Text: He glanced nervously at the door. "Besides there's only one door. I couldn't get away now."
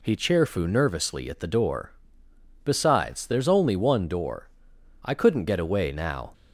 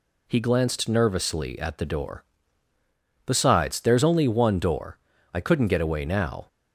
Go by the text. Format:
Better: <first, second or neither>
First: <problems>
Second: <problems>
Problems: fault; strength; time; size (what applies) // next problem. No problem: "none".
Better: second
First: says "cheerfu" for "glanced"; at 0.1 s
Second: none